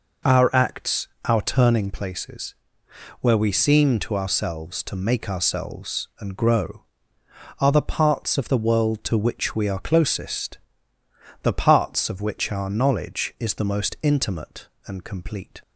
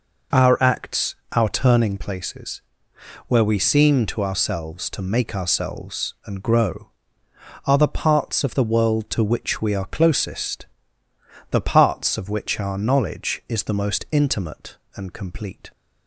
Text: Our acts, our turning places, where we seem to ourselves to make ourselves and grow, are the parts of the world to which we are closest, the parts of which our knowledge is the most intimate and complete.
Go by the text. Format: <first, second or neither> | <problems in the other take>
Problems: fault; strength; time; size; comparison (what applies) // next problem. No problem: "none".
neither | none